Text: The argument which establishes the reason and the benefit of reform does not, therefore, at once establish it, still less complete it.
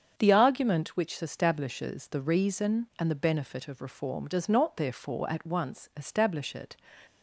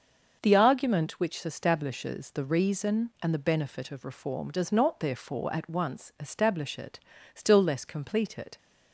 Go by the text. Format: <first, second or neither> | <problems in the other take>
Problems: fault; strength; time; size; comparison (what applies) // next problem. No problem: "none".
second | starts louder than the rest; strong; until 1.1 s; 7.5 dB; also in the second // stops before "still less complete it"; at 7.0 s